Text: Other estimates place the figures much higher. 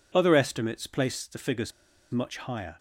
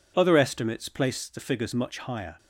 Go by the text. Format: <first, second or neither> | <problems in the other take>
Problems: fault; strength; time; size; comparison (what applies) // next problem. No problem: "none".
second | pauses between "figures" and "much"; at 1.7 s; 0.40 s long